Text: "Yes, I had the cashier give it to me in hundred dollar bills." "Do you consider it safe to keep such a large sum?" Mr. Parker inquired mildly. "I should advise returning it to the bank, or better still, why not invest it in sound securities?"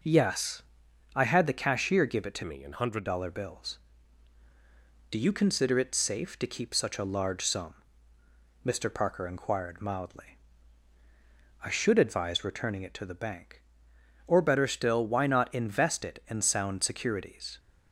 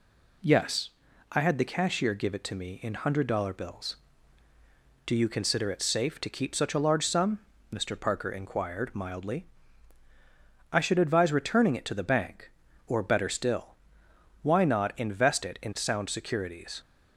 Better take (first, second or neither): second